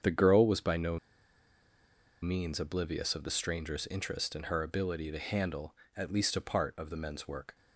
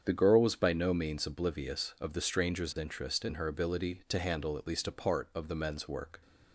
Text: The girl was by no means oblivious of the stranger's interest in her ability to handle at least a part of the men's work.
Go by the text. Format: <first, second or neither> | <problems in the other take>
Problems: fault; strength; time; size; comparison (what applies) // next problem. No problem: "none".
second | starts louder than the rest; strong; until 2.2 s; 7.5 dB; strong in the second // pauses between "no" and "means"; at 0.9 s; 1.2 s long